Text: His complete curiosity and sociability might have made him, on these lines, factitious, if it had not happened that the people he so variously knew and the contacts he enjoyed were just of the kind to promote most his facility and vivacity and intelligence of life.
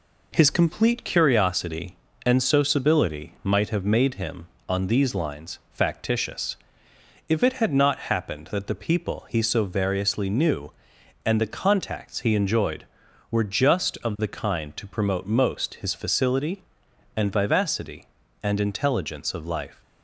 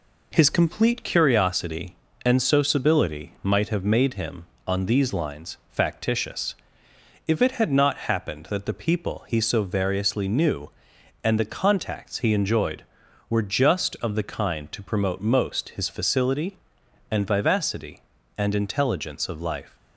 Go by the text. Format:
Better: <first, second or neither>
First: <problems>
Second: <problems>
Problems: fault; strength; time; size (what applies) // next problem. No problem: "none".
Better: neither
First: none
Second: none